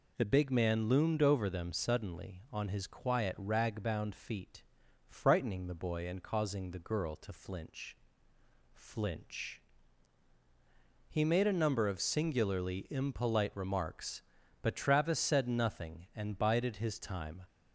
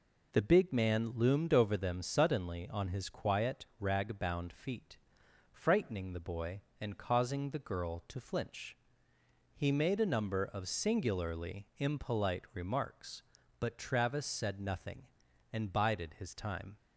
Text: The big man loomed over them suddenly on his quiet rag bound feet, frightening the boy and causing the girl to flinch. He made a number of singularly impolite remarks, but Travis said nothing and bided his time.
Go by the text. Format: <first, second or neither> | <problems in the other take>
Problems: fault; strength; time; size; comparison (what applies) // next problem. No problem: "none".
second | says "flinch" twice; at 8.7 s